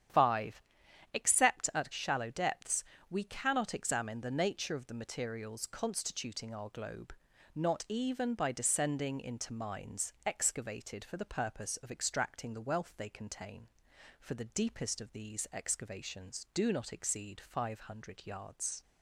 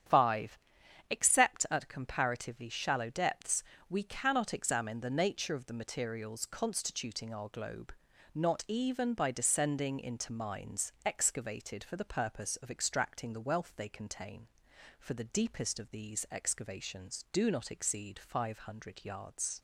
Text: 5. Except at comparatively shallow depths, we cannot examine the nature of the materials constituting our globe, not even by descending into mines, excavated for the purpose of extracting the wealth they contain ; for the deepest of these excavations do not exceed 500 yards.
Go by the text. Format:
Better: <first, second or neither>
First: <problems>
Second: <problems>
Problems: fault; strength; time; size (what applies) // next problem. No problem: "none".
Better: second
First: starts louder than the rest; strong; until 1.6 s; 9.5 dB // skips "comparatively"; at 1.9 s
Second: starts louder than the rest; strong; until 1.6 s; 9 dB